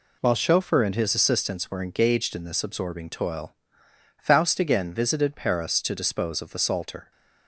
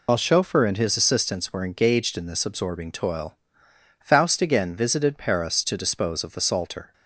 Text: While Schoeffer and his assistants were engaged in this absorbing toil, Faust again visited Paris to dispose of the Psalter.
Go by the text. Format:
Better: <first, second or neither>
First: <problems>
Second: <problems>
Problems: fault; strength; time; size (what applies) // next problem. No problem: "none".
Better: first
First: none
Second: loses the start of "While"; at 0.0 s; 60 ms